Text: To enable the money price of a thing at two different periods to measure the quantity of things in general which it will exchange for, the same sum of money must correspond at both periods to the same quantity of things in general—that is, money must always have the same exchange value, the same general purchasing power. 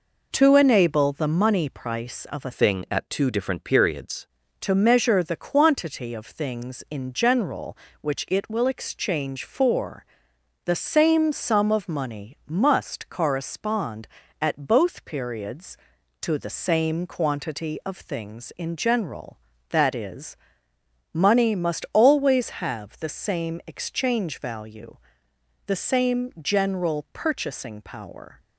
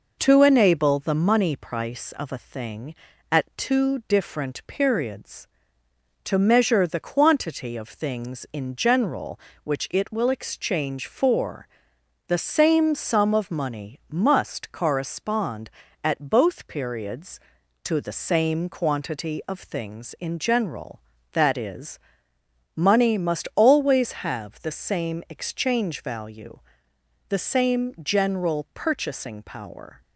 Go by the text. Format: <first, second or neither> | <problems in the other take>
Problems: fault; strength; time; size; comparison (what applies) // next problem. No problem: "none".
second | changes voice from "thing" to "periods"; from 2.5 to 4.2 s; 1.7 s long